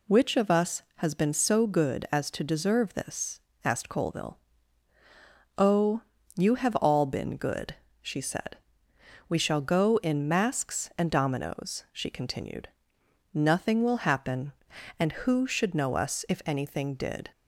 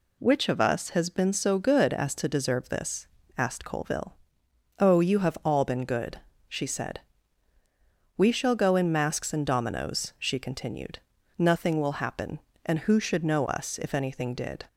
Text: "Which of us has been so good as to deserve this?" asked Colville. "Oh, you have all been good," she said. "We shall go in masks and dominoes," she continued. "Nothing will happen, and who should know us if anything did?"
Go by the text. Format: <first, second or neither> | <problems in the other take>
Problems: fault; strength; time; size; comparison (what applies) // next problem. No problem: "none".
neither | none